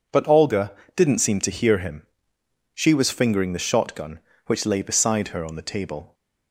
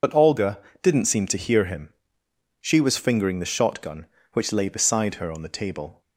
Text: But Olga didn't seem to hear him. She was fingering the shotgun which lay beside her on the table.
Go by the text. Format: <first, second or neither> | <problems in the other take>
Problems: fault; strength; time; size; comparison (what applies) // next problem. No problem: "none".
first | loses the start of "But"; at 0.0 s; 70 ms // pauses between "Olga" and "didn't"; slight; at 0.5 s; 0.24 s long; slight in the first